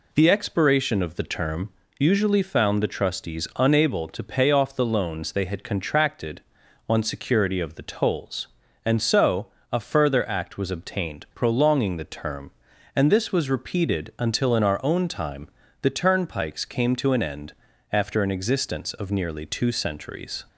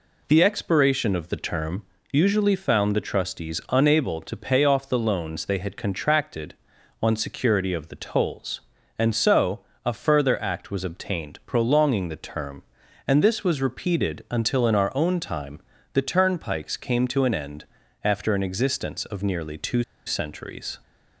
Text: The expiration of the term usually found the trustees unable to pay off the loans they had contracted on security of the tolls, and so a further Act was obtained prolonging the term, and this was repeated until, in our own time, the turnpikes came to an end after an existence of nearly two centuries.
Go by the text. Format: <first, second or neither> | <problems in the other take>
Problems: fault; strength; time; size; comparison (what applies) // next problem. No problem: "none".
first | pauses between "term" and "usually"; slight; at 1.8 s; 0.28 s long; slight in the first // pauses between "so" and "a"; slight; at 9.6 s; 0.24 s long; slight in the first // pauses between "end" and "after"; slight; at 17.6 s; 0.36 s long; slight in the first // pauses between "two" and "centuries"; slight; at 19.8 s; 0.24 s long